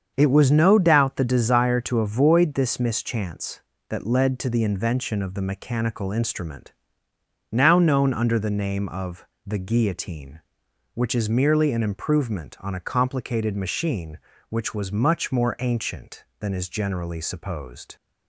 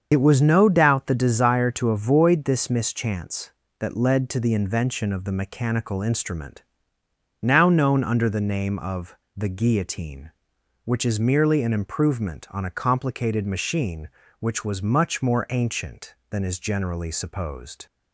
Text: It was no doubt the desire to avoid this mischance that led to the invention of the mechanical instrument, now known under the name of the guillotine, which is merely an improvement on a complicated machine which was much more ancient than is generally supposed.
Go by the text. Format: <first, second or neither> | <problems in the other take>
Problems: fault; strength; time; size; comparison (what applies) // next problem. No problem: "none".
first | loses the start of "It"; at 0.1 s; 60 ms // starts louder than the rest; until 1.1 s; 7 dB; also in the first // pauses between "of" and "the"; slight; at 9.1 s; 0.18 s long; slight in the first